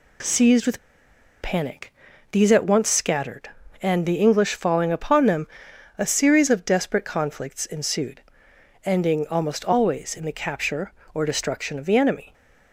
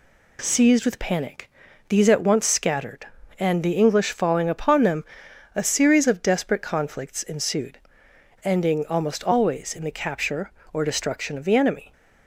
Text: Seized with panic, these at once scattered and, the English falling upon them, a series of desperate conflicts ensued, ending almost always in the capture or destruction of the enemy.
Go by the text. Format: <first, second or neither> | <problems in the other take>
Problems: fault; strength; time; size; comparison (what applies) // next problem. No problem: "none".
second | pauses between "with" and "panic"; noticeable; at 0.7 s; 0.62 s long